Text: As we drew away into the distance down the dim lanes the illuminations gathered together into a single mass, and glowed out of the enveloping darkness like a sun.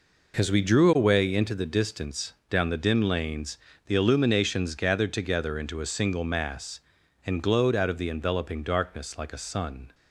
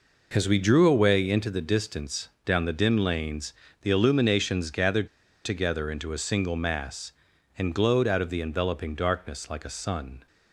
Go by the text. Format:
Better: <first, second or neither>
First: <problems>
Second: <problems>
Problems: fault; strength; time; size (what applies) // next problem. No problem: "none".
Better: first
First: pauses between "distance" and "down"; slight; at 2.3 s; 0.16 s long // pauses between "lanes" and "the"; slight; at 3.5 s; 0.30 s long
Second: pauses between "distance" and "down"; slight; at 2.2 s; 0.16 s long // pauses between "lanes" and "the"; slight; at 3.5 s; 0.30 s long // pauses between "gathered" and "together"; at 5.0 s; 0.38 s long